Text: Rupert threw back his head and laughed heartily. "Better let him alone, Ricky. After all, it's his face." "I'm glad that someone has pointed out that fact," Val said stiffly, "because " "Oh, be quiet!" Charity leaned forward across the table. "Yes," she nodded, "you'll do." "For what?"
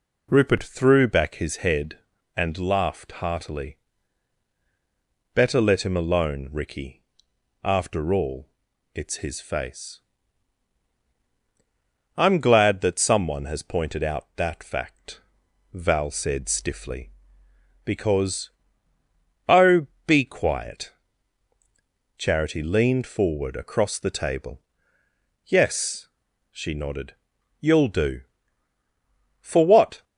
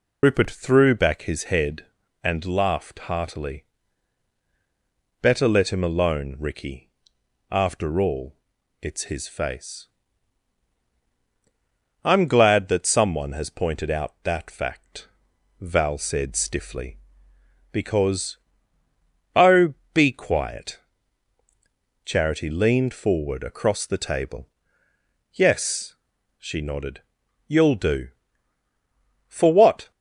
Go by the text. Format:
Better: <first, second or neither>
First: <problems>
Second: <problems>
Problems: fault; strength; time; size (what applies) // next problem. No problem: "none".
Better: first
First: none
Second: loses the start of "Rupert"; at 0.2 s; 75 ms